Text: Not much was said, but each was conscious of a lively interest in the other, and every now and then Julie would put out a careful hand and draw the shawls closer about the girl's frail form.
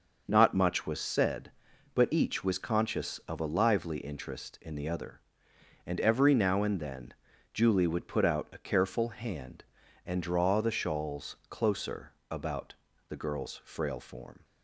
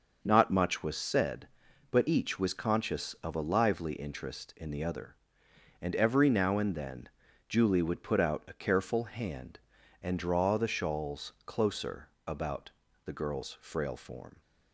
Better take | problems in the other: neither | starts louder than the rest; the same in both // pauses between "then" and "Julie"; the same in both // pauses between "closer" and "about"; slight; the same in both // pauses between "about" and "the"; slight; the same in both

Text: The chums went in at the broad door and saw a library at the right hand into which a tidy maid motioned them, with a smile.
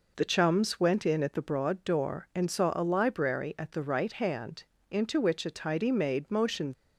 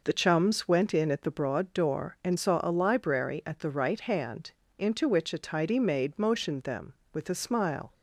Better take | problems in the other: second | pauses between "hand" and "into"; slight; at 4.6 s; 0.28 s long; slight in the second // stops before "them with a smile"; at 6.7 s

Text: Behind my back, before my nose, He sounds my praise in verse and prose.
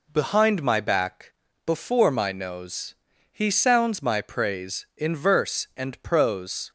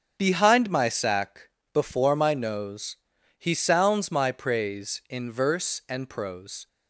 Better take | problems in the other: first | starts louder than the rest; strong; until 1.2 s; 7.5 dB // says "sack" for "back"; at 0.8 s

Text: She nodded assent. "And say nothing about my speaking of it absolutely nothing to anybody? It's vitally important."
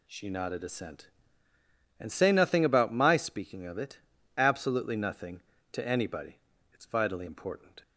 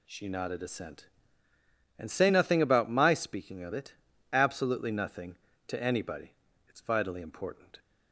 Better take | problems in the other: neither | pauses between "it" and "absolutely"; the same in both

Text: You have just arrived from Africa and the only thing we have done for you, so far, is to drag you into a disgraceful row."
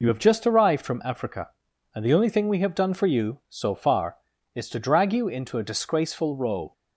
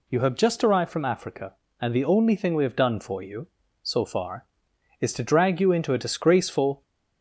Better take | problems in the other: first | stops before "row"; at 6.8 s

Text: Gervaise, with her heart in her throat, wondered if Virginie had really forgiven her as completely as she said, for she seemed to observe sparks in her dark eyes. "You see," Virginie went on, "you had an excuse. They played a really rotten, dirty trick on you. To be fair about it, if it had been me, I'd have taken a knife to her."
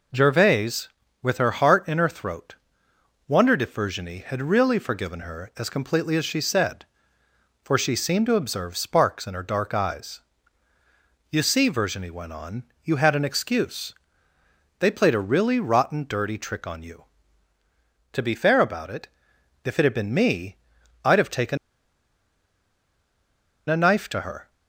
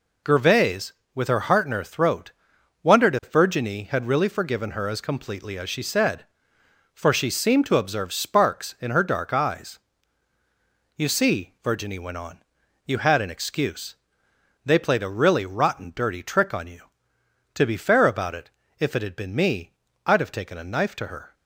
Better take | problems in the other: second | pauses between "taken" and "a"; strong; at 21.5 s; 2.1 s long

